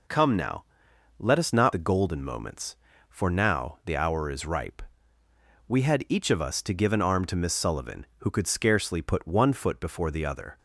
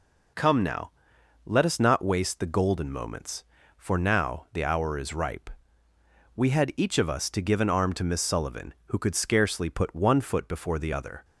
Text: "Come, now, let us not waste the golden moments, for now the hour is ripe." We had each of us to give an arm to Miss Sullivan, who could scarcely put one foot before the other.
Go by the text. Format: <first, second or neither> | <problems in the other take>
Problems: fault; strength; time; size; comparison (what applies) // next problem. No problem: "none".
second | skips "waste"; at 1.7 s